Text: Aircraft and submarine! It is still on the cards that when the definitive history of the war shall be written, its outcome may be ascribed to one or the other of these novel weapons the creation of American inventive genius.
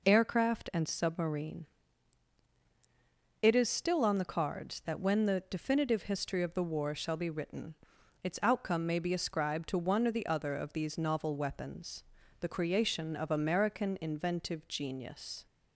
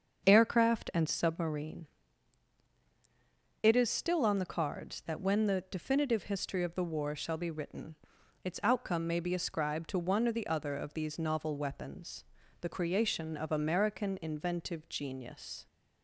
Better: first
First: pauses between "weapons" and "the"; at 12.0 s; 0.38 s long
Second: starts louder than the rest; until 1.5 s; 6.5 dB // pauses between "weapons" and "the"; at 12.2 s; 0.38 s long

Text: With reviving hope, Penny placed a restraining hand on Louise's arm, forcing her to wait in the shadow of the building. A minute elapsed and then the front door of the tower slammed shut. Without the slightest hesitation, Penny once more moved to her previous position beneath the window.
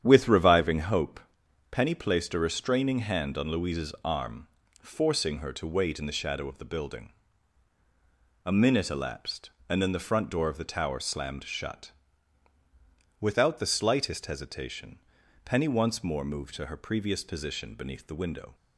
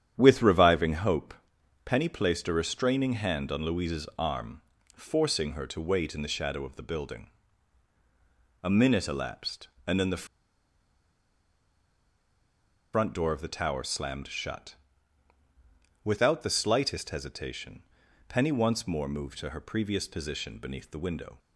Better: first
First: starts louder than the rest; strong; until 1.0 s; 9 dB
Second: starts louder than the rest; strong; until 1.1 s; 9 dB // pauses between "the" and "front"; strong; at 10.2 s; 2.6 s long

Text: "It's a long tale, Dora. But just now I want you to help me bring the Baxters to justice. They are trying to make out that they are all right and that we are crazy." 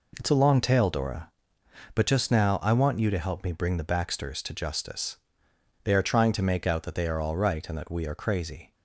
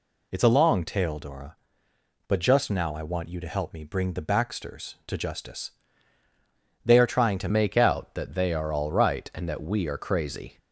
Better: first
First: none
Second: changes voice at "make"; from 7.4 s on; 3.1 s long

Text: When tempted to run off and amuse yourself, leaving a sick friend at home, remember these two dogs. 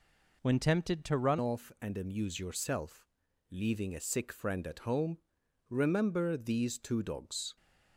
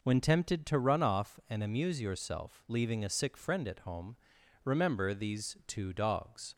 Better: second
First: changes voice at "off"; from 1.3 s on; 6.2 s long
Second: none

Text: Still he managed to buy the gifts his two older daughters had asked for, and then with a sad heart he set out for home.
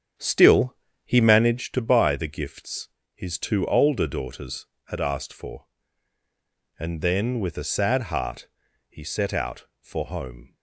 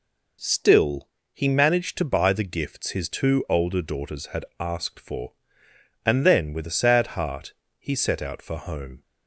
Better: second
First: starts louder than the rest; strong; until 1.7 s; 8 dB // pauses between "Still" and "he"; slight; at 0.7 s; 0.28 s long // pauses between "gifts" and "his"; slight; at 2.8 s; 0.26 s long // pauses between "heart" and "he"; at 8.4 s; 0.42 s long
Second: pauses between "Still" and "he"; slight; at 1.0 s; 0.24 s long // pauses between "heart" and "he"; slight; at 7.5 s; 0.26 s long

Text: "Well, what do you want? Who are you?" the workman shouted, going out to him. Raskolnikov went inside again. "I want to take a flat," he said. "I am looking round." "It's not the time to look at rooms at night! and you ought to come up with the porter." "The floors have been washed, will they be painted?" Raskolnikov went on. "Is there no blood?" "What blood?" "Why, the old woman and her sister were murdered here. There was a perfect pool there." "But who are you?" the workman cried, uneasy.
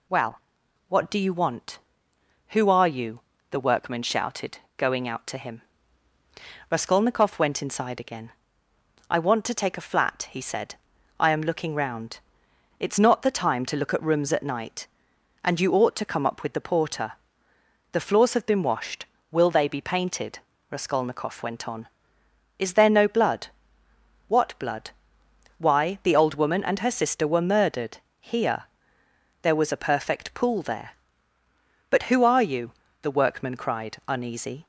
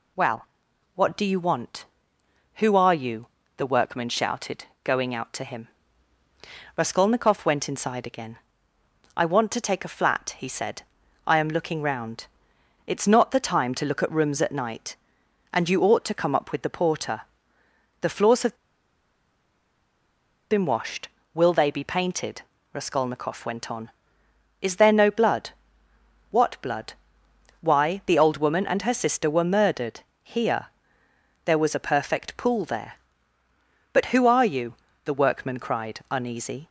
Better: first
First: pauses between "murdered" and "here"; slight; at 27.9 s; 0.22 s long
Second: pauses between "have" and "been"; strong; at 18.5 s; 1.9 s long // pauses between "murdered" and "here"; slight; at 30.0 s; 0.22 s long

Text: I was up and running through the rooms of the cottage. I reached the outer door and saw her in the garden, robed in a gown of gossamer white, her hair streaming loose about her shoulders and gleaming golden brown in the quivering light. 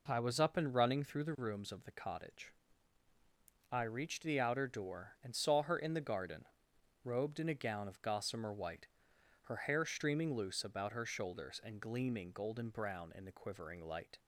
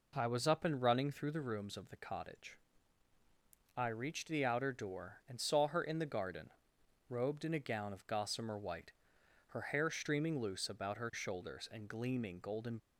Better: first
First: none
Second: stops before "brown in the quivering light"; at 12.7 s

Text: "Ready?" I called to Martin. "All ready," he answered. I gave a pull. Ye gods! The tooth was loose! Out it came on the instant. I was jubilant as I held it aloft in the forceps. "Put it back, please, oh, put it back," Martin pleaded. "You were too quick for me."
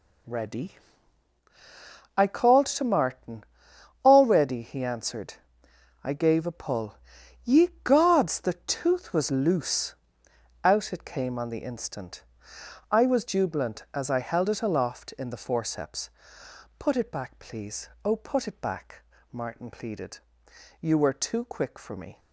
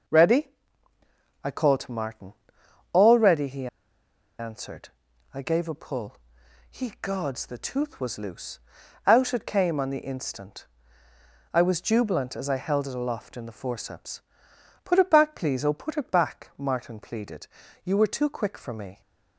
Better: first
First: none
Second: pauses between "he" and "answered"; noticeable; at 3.6 s; 0.72 s long

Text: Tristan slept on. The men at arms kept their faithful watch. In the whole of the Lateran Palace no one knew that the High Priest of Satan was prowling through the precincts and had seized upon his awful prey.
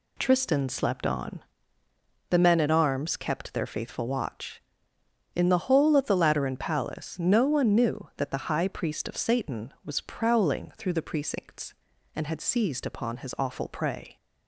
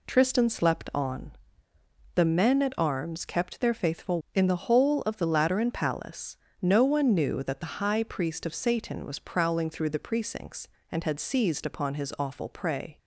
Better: first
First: none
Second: skips "watch"; at 4.2 s // pauses between "Palace" and "no"; slight; at 6.3 s; 0.26 s long

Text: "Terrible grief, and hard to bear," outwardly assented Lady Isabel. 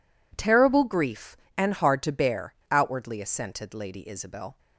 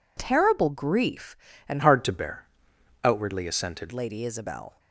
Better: first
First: none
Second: changes voice from "hard" to "assented"; from 1.8 to 3.9 s; 2.1 s long

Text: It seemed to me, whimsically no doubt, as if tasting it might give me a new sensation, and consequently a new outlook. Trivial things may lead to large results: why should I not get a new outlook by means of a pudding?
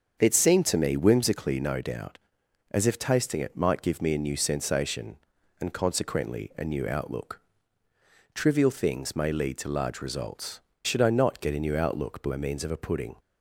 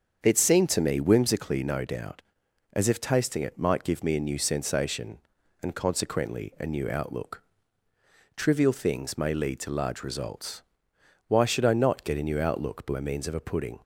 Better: second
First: starts louder than the rest; until 1.2 s; 7 dB // skips "why"; at 10.7 s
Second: starts louder than the rest; until 1.2 s; 7 dB

